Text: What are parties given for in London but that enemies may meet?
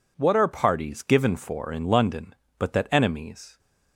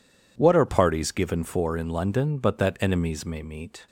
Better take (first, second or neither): second